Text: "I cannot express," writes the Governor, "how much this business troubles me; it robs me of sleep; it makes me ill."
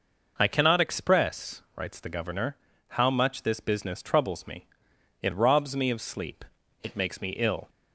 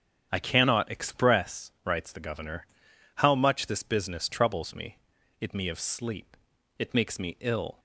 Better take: first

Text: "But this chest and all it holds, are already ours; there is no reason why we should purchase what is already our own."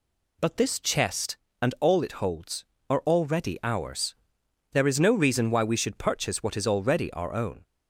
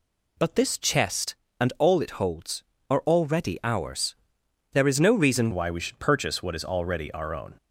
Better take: first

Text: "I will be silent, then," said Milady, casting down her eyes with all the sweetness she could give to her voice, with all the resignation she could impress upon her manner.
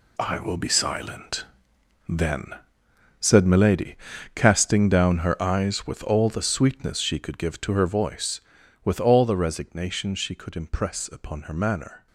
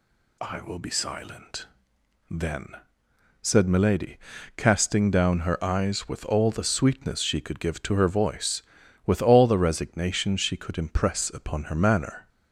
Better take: second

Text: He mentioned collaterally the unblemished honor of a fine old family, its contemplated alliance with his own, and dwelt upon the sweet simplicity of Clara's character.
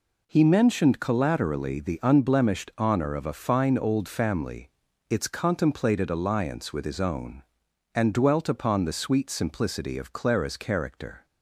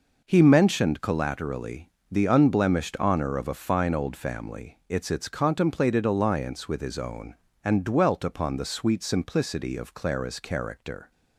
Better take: first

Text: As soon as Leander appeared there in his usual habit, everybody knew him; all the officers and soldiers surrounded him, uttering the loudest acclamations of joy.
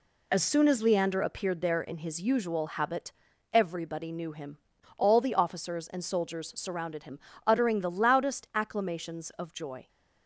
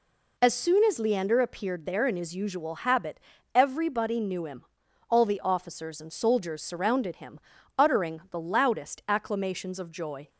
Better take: neither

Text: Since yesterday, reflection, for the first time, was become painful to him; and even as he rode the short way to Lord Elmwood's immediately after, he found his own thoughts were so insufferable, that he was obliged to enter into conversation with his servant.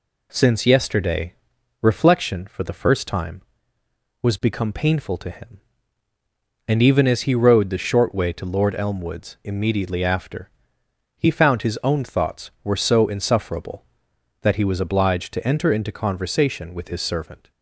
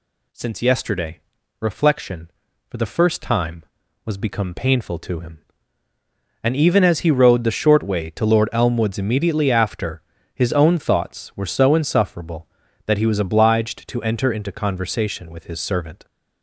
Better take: first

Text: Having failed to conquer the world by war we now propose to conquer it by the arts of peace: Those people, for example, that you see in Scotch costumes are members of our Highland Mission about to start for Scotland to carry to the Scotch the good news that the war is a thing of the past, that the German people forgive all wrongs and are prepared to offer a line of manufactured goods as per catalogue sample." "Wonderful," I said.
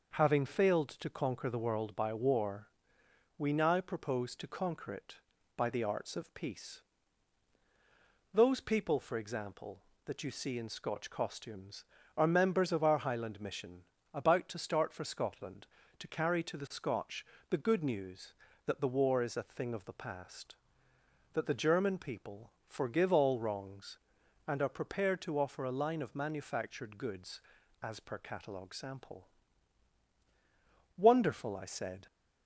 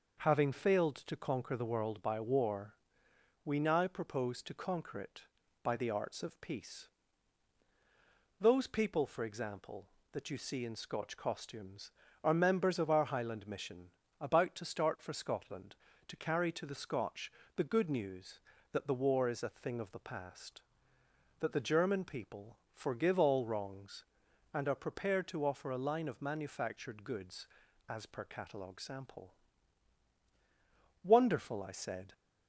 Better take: neither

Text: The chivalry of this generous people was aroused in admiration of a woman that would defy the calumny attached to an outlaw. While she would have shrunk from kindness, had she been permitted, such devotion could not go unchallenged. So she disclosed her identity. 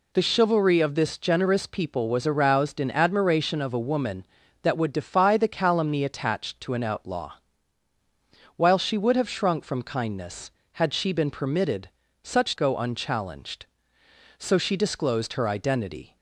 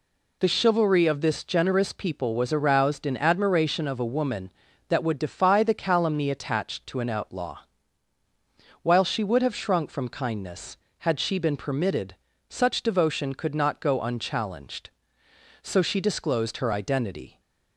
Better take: second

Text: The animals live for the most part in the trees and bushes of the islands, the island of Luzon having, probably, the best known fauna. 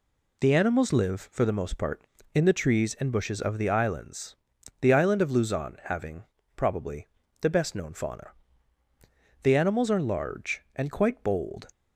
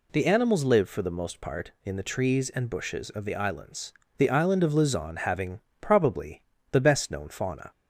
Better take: second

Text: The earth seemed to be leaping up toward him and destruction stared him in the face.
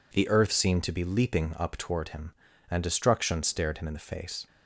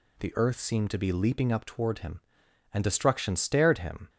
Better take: first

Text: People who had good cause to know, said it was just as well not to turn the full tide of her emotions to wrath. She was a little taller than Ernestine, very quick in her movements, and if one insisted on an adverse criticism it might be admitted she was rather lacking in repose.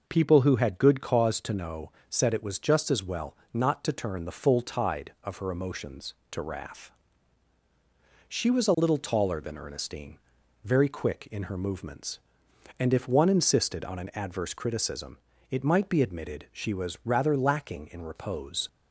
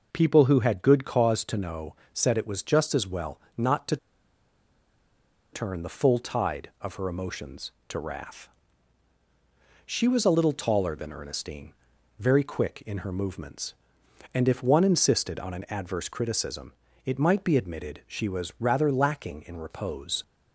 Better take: first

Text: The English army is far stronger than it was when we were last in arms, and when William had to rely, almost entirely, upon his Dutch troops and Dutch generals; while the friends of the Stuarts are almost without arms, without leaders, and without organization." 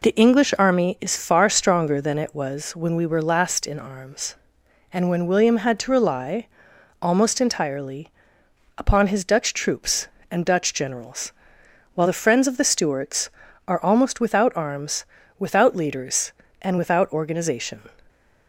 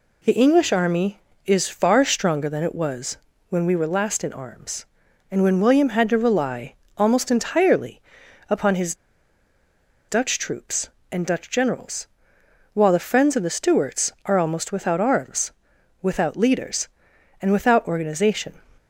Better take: first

